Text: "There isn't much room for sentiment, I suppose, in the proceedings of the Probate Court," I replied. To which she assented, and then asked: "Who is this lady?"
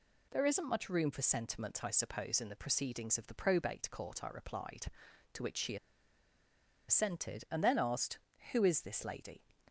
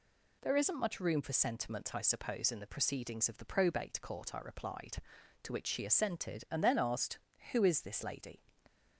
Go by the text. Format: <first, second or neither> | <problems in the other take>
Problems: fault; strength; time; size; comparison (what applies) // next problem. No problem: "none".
second | pauses between "she" and "assented"; at 5.7 s; 1.1 s long